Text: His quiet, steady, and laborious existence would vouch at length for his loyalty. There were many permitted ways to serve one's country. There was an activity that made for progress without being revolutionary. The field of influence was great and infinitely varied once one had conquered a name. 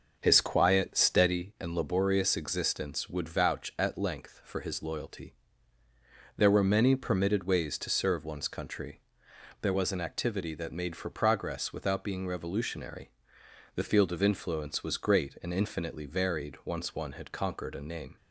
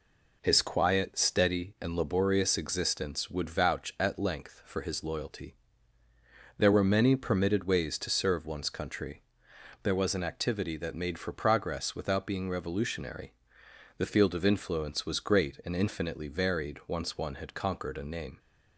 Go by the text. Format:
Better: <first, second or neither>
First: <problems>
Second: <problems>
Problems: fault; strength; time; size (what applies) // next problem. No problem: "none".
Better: second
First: starts louder than the rest; noticeable; until 1.5 s; 6 dB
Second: none